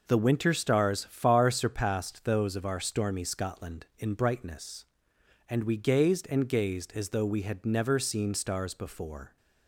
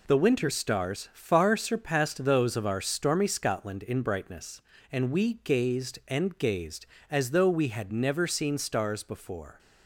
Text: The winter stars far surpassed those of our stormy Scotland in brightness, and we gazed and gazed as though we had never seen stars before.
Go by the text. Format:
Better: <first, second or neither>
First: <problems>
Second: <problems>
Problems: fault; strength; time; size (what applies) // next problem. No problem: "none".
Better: first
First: none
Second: loses the start of "The"; at 0.0 s; 25 ms